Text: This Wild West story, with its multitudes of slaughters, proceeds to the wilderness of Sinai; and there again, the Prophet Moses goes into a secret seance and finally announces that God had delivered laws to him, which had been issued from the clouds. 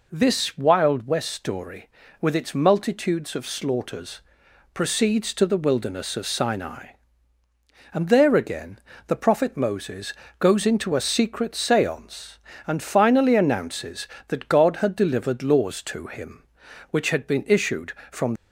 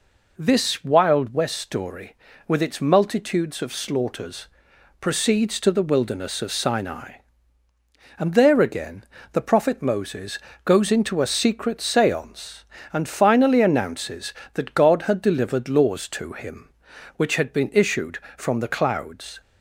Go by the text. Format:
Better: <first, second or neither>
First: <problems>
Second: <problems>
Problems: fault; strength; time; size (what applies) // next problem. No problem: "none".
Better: second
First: pauses between "Moses" and "goes"; slight; at 10.1 s; 0.26 s long // stops before "the clouds"; at 18.3 s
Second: pauses between "Moses" and "goes"; slight; at 10.3 s; 0.26 s long